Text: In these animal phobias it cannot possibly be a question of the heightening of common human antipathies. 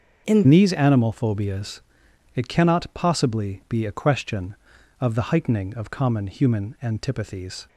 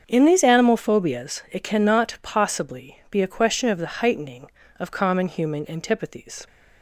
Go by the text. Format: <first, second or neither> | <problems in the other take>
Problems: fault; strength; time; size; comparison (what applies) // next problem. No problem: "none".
second | starts louder than the rest; until 1.3 s; 6.5 dB; strong in the second // changes voice at "these"; from 0.4 s on; 7.2 s long // pauses between "phobias" and "it"; noticeable; at 1.8 s; 0.54 s long